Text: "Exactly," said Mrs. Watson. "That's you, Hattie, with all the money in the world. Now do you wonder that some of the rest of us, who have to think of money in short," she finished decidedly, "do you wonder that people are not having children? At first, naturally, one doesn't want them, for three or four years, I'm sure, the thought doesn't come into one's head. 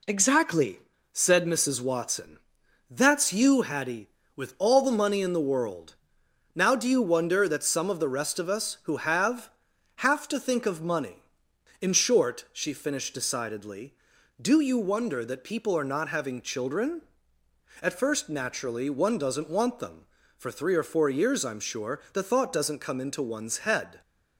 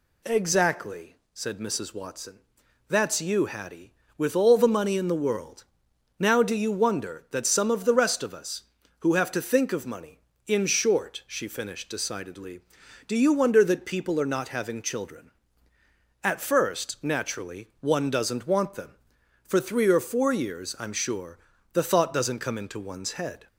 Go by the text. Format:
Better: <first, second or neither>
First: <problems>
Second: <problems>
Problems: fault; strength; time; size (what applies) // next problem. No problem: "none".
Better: second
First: says "have" twice; at 9.9 s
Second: none